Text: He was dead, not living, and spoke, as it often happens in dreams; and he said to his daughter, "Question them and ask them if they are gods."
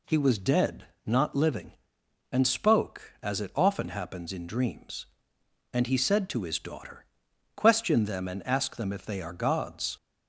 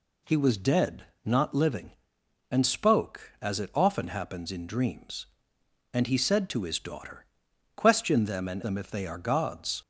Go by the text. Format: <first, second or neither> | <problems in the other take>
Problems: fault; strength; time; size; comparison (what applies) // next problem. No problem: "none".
first | skips "ask"; at 8.6 s